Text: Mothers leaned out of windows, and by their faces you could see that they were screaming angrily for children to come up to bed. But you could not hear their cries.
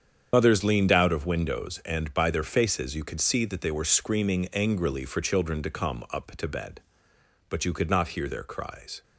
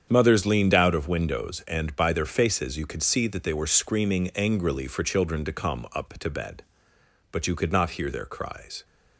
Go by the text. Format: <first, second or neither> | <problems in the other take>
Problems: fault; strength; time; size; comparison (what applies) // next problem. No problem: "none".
second | loses the start of "Mothers"; at 0.3 s; 60 ms // starts louder than the rest; strong; until 1.3 s; 8 dB; strong in the second